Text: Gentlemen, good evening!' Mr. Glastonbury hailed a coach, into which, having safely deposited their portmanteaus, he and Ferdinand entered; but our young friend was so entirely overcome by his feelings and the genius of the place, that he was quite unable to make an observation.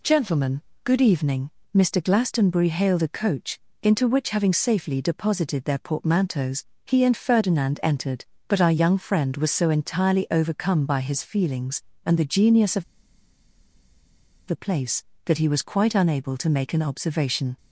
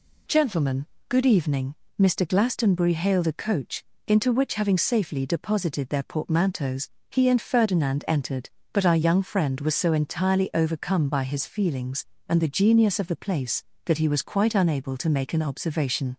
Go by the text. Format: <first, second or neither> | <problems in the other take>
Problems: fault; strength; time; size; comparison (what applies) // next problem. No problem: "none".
second | pauses between "of" and "the"; strong; at 12.8 s; 1.6 s long